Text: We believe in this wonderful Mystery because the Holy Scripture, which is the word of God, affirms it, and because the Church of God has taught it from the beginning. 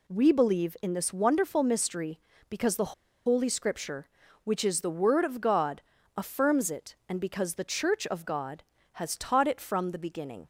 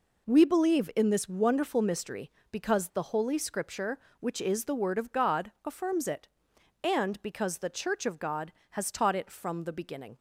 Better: second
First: pauses between "the" and "Holy"; slight; at 2.9 s; 0.33 s long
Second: none

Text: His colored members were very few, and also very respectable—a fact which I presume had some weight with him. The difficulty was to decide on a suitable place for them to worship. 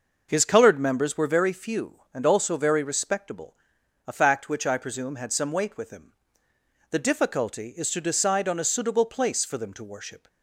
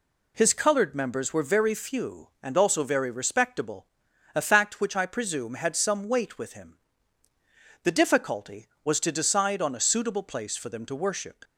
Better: second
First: says "is" for "was"; at 7.7 s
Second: none

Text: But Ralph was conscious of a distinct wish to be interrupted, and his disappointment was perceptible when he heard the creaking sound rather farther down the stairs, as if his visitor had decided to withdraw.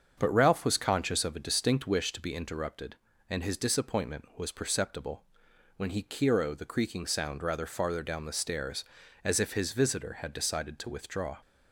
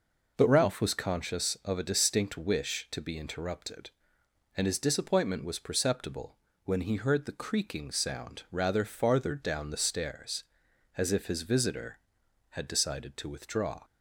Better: second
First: starts louder than the rest; until 1.1 s; 7 dB // pauses between "perceptible" and "when"; noticeable; at 5.2 s; 0.54 s long // says "kiro" for "heard"; at 6.0 s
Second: pauses between "perceptible" and "when"; slight; at 6.3 s; 0.28 s long

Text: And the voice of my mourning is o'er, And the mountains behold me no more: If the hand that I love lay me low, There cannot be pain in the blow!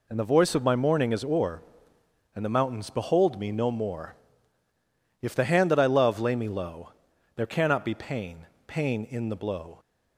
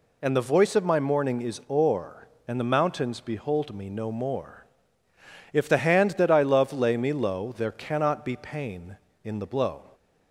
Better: second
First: says "pain" twice; at 8.6 s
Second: none

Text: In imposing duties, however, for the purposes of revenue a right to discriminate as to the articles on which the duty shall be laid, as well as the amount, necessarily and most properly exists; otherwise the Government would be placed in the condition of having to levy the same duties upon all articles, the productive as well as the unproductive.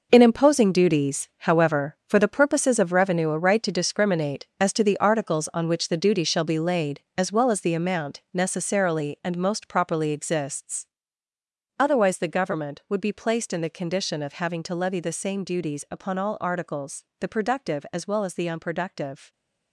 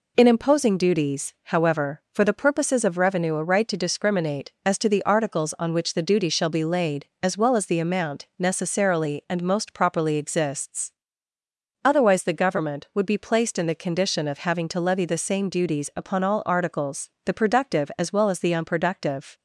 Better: second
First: gets quieter; strong; throughout; 10.5 dB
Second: none

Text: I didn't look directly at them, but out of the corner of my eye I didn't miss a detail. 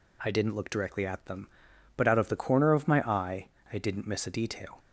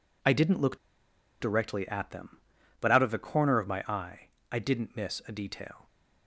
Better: first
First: pauses between "eye" and "I"; slight; at 3.4 s; 0.24 s long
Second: pauses between "look" and "directly"; noticeable; at 0.7 s; 0.63 s long // pauses between "eye" and "I"; slight; at 4.2 s; 0.22 s long

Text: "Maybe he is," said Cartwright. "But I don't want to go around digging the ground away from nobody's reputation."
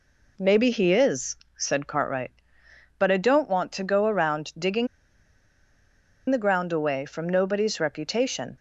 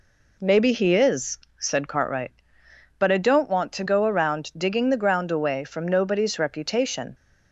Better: second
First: pauses between "digging" and "the"; strong; at 4.8 s; 1.4 s long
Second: none

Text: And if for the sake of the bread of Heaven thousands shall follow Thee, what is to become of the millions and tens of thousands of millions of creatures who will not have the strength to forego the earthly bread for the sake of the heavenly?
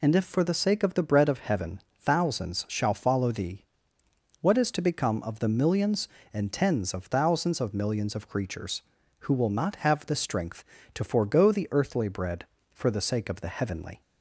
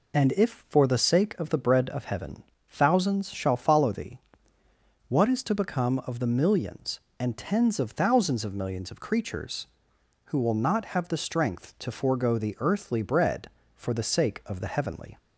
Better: neither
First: pauses between "Heaven" and "thousands"; slight; at 1.8 s; 0.18 s long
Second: pauses between "Heaven" and "thousands"; slight; at 2.4 s; 0.26 s long

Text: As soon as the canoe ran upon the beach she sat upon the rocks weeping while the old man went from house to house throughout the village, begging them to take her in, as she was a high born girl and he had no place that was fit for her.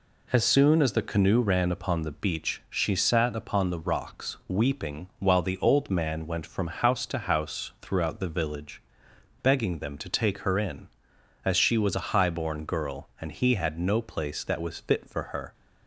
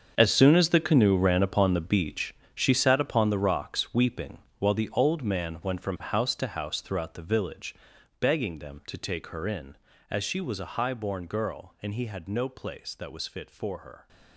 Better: first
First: none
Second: gets quieter; strong; throughout; 14 dB // pauses between "beach" and "she"; slight; at 2.3 s; 0.18 s long // pauses between "weeping" and "while"; slight; at 4.3 s; 0.20 s long

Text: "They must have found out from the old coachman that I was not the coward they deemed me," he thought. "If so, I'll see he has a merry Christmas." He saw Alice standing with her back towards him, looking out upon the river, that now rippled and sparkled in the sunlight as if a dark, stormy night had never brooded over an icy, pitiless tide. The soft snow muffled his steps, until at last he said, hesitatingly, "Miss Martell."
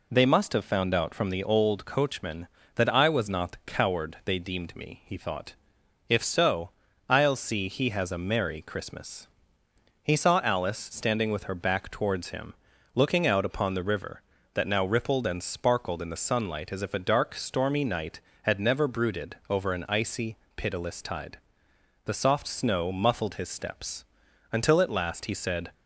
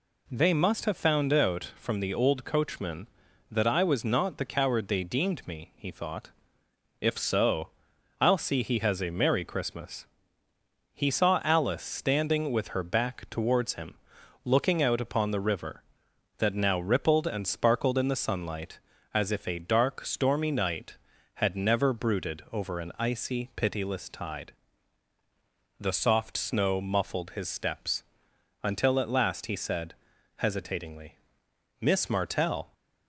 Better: second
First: stops before "hesitatingly Miss Martell"; at 25.7 s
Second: none

